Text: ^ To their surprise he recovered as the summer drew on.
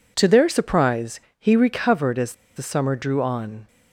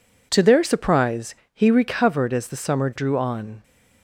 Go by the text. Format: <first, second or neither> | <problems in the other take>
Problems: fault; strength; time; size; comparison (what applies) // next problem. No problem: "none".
second | pauses between "surprise" and "he"; slight; at 1.1 s; 0.22 s long; slight in the second // pauses between "as" and "the"; slight; at 2.3 s; 0.21 s long